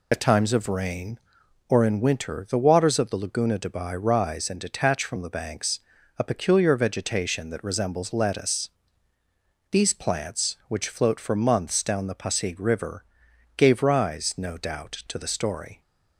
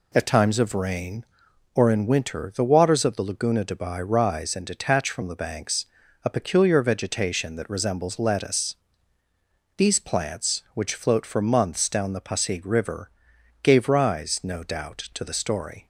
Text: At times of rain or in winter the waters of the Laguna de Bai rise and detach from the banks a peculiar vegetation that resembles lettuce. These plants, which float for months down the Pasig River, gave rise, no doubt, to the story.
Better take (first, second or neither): second